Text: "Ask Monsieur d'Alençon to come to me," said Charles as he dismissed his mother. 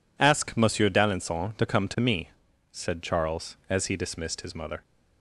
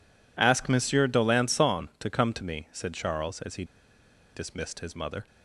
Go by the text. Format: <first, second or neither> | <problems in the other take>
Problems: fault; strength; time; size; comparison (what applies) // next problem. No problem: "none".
first | pauses between "he" and "dismissed"; noticeable; at 3.6 s; 0.70 s long